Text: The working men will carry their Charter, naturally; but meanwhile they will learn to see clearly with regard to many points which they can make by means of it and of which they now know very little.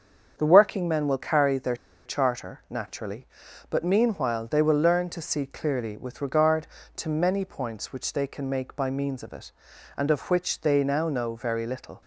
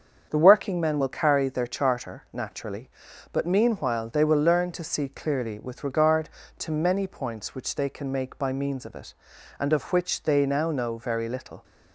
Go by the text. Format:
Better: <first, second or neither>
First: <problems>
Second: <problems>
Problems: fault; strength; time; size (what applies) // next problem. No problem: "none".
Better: second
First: starts louder than the rest; until 1.3 s; 7 dB // pauses between "their" and "Charter"; slight; at 1.7 s; 0.30 s long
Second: starts louder than the rest; until 1.3 s; 7 dB